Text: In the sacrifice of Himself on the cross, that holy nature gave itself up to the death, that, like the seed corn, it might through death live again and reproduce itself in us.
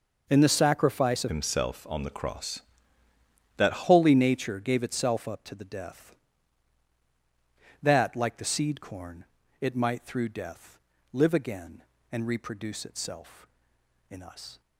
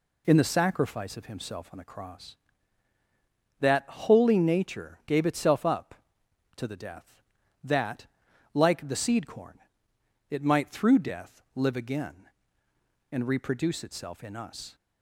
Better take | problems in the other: second | changes voice from "Himself" to "that"; from 1.2 to 3.8 s; 2.6 s long // pauses between "death" and "live"; slight; at 10.7 s; 0.34 s long

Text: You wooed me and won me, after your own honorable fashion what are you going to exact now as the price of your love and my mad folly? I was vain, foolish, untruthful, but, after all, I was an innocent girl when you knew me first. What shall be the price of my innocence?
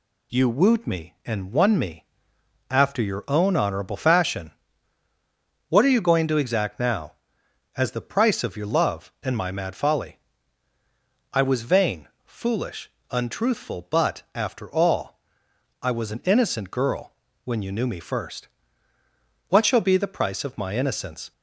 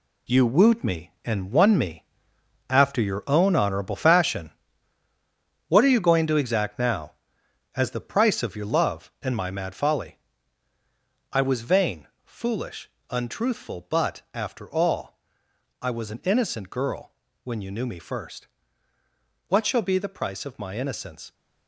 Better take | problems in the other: first | gets quieter; strong; throughout; 9.5 dB // pauses between "fashion" and "what"; at 4.5 s; 1.1 s long; also in the first // pauses between "girl" and "when"; slight; at 17.1 s; 0.32 s long; slight in the first

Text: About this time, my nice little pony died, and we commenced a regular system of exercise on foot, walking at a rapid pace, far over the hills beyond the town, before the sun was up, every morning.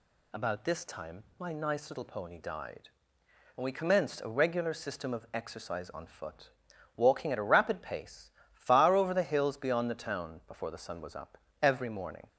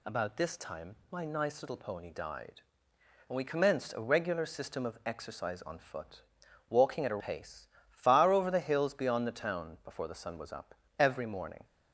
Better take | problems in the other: first | skips "rapid"; at 7.2 s

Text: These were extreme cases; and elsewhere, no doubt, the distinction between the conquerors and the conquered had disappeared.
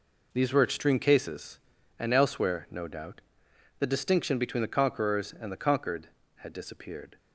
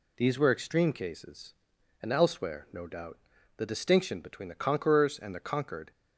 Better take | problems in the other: first | stops before "had disappeared"; at 5.9 s

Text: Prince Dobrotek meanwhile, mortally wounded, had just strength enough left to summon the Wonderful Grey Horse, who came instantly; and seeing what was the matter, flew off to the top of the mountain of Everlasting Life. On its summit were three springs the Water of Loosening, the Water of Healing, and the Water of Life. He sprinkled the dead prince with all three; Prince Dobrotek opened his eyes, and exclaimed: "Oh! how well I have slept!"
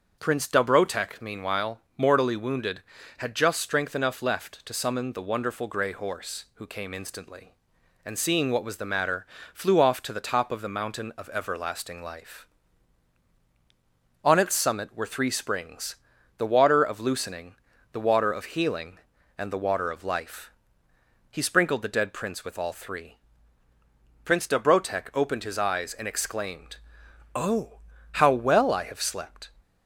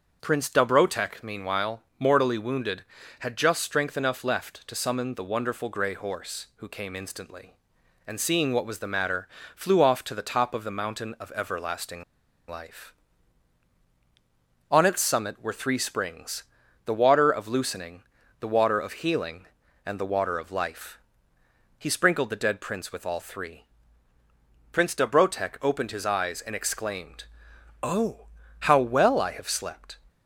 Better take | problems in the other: first | starts louder than the rest; until 1.2 s; 6.5 dB; also in the first // pauses between "Everlasting" and "Life"; at 12.0 s; 0.45 s long // pauses between "springs" and "the"; at 16.4 s; 0.42 s long; also in the first

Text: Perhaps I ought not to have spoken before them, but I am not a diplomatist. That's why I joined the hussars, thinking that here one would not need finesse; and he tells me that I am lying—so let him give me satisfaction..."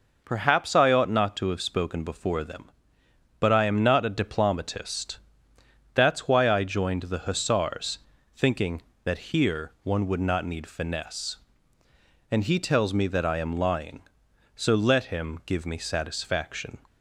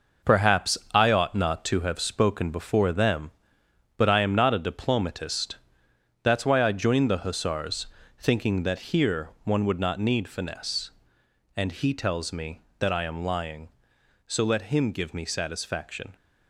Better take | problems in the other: first | gets quieter; strong; throughout; 7.5 dB // pauses between "Perhaps" and "I"; slight; at 0.7 s; 0.16 s long

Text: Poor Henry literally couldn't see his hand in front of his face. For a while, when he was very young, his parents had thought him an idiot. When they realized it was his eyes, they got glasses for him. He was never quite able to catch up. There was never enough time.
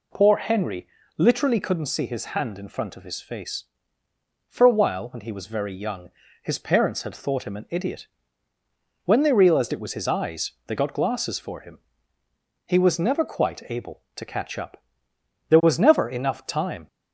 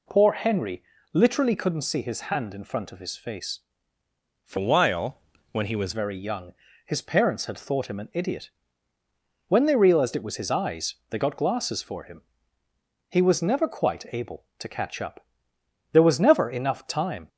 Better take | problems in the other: first | pauses between "Henry" and "literally"; slight; at 0.8 s; 0.30 s long; slight in the first // changes voice from "a" to "was"; from 4.5 to 5.9 s; 1.4 s long

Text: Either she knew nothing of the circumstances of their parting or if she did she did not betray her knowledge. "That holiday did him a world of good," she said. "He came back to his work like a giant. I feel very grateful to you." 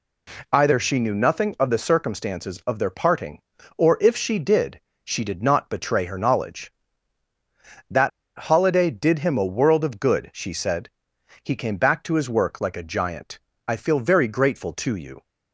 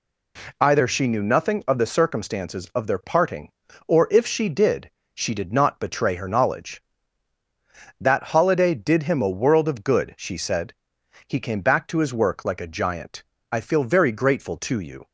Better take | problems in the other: second | pauses between "did" and "she"; slight; at 4.7 s; 0.24 s long; slight in the second // pauses between "That" and "holiday"; slight; at 8.1 s; 0.28 s long

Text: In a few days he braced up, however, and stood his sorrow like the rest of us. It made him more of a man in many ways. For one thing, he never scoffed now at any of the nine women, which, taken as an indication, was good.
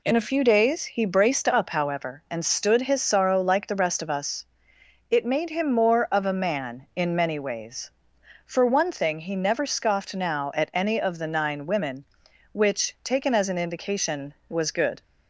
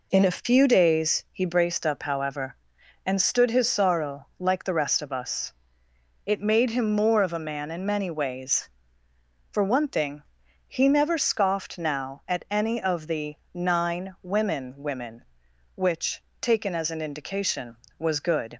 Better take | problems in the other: first | pauses between "the" and "nine"; slight; at 13.3 s; 0.18 s long // says "women" twice; at 14.7 s

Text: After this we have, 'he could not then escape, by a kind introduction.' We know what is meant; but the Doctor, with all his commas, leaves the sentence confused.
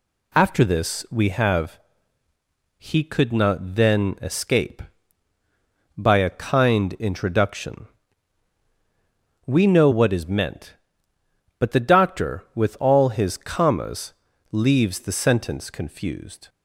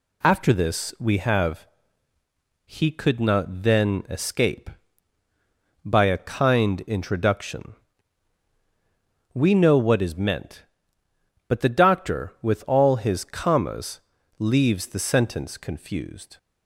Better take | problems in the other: neither | none

